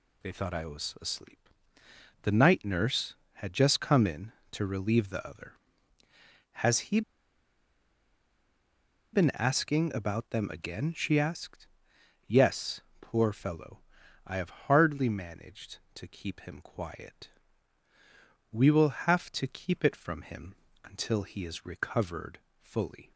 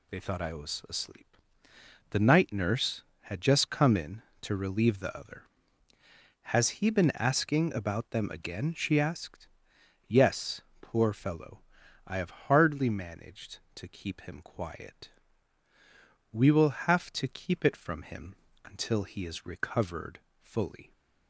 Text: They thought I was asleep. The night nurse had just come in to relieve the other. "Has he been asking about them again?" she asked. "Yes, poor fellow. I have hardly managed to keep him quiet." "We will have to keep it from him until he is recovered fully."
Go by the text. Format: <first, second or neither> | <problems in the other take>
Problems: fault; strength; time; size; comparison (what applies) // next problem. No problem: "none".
second | pauses between "he" and "been"; strong; at 7.0 s; 2.1 s long // pauses between "him" and "until"; slight; at 20.5 s; 0.28 s long; slight in the second // pauses between "recovered" and "fully"; slight; at 22.3 s; 0.20 s long; slight in the second